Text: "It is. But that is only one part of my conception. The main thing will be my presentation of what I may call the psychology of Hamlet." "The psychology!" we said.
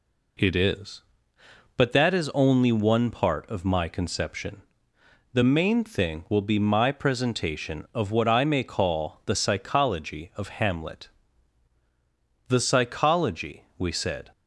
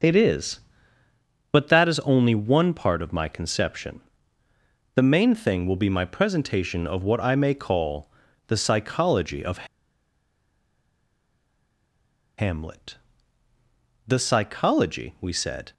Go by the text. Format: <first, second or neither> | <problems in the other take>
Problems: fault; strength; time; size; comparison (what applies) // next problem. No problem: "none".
first | starts louder than the rest; until 1.9 s; 6 dB // pauses between "call" and "the"; at 8.1 s; 0.38 s long // pauses between "of" and "Hamlet"; strong; at 9.6 s; 2.7 s long